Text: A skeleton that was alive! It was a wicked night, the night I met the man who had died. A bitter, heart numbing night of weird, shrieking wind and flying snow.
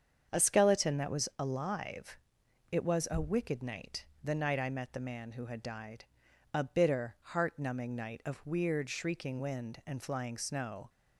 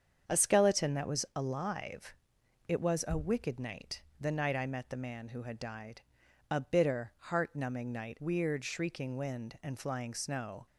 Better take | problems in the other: first | starts louder than the rest; strong; until 1.4 s; 7.5 dB; strong in the first // skips "of"; at 8.1 s

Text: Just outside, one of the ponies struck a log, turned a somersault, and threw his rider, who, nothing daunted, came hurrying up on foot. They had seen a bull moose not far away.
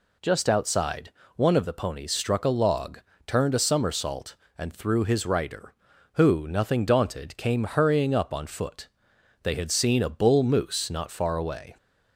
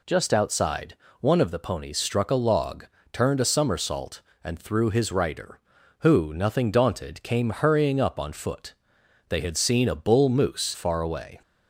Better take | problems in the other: first | skips "not"; at 10.7 s

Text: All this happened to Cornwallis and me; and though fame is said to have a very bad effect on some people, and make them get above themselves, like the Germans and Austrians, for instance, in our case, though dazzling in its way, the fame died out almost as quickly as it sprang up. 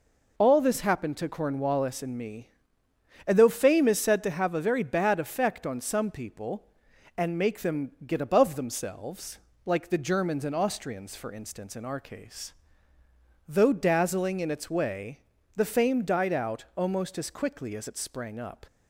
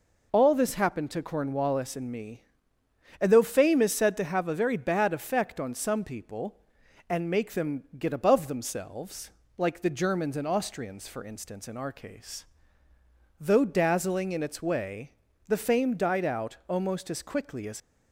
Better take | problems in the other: first | stops before "it sprang up"; at 17.7 s

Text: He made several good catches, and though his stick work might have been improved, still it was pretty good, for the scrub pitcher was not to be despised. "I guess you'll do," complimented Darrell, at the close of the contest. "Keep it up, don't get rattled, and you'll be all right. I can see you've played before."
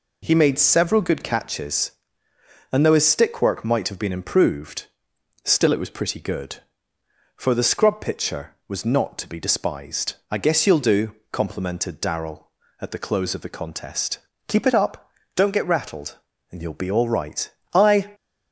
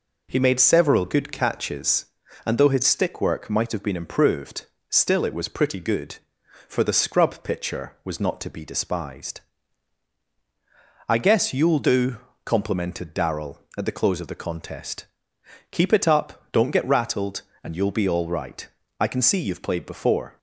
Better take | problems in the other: second | stops before "can see you've played before"; at 18.1 s

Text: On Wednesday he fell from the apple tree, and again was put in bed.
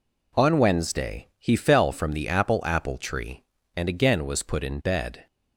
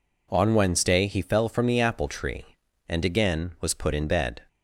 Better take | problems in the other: second | says "apple" twice; at 2.6 s

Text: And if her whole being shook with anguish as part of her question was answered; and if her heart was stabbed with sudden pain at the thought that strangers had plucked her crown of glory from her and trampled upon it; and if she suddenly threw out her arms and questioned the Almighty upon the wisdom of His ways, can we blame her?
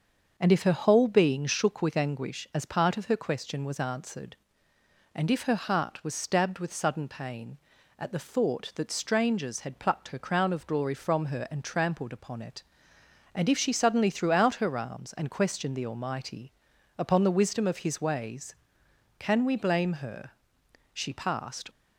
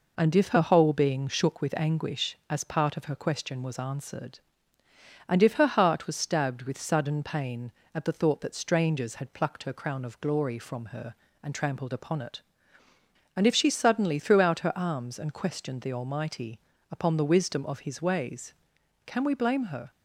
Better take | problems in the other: second | starts louder than the rest; until 1.3 s; 6.5 dB // pauses between "Almighty" and "upon"; at 16.5 s; 0.42 s long; slight in the second // goes on to say "She passed"; noticeable; from 20.9 s on; 0.74 s long

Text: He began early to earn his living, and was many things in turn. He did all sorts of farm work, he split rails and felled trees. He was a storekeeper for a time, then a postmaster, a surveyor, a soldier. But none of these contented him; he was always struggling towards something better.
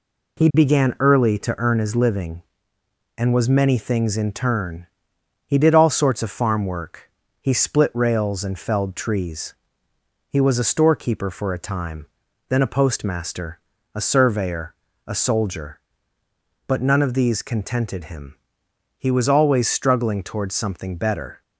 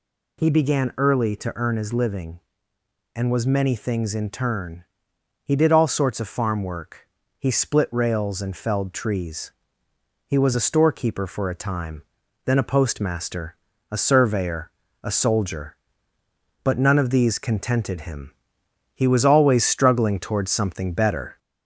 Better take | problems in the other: first | gets louder; slight; throughout; 2 dB

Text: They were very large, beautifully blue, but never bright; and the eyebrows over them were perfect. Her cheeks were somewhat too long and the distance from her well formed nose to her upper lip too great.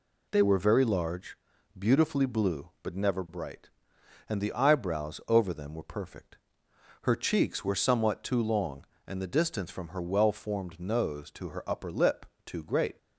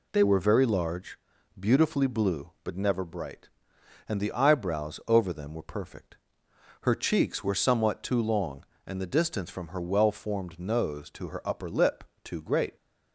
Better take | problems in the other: neither | pauses between "lip" and "too"; slight; the same in both

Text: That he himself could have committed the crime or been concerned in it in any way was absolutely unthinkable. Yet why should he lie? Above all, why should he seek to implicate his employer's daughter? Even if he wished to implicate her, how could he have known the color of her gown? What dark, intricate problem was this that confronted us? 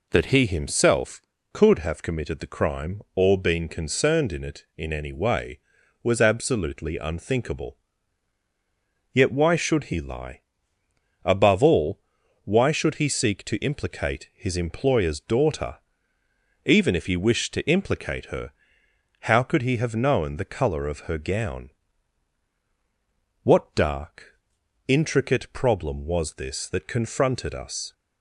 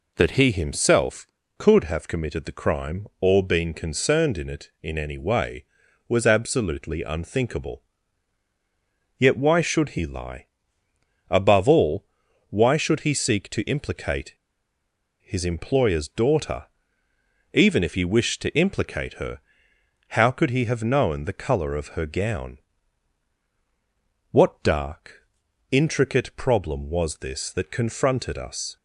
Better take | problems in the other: first | pauses between "implicate" and "his"; noticeable; at 14.3 s; 0.88 s long

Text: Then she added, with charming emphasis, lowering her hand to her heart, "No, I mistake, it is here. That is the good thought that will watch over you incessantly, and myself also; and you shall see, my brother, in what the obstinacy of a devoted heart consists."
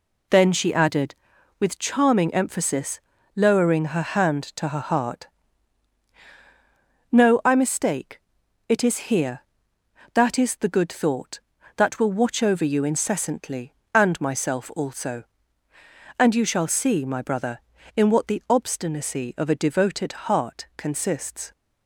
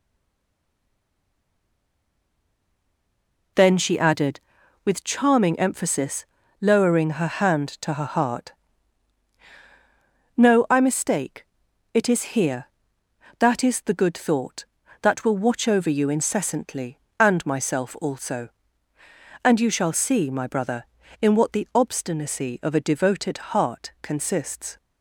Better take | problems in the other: first | stays silent before the first word; strong; until 3.5 s; 3.5 s long // pauses between "devoted" and "heart"; slight; at 23.3 s; 0.16 s long; slight in the first

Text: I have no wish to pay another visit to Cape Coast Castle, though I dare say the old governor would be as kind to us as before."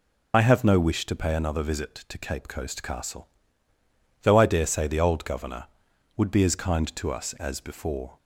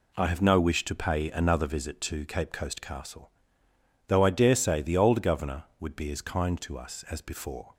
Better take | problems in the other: second | loses the start of "I"; at 0.3 s; 40 ms

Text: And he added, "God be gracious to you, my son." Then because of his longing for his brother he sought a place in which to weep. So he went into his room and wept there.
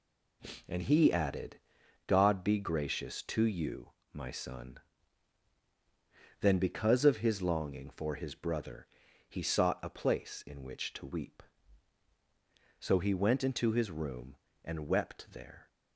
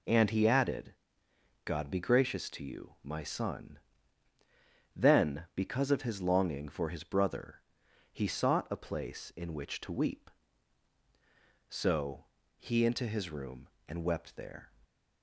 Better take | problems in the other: first | pauses between "brother" and "he"; noticeable; at 7.6 s; 0.50 s long; also in the first // pauses between "So" and "he"; slight; at 12.2 s; 0.32 s long // skips "went"; at 12.8 s

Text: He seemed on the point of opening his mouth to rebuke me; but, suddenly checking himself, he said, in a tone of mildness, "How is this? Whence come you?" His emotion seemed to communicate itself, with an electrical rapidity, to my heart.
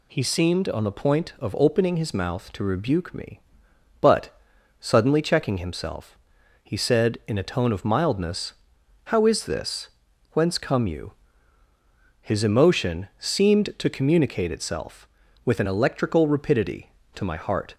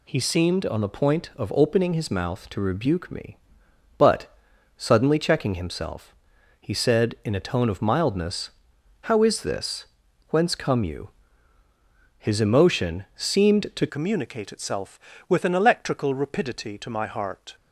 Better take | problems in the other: first | changes voice at "communicate"; from 13.8 s on; 3.7 s long

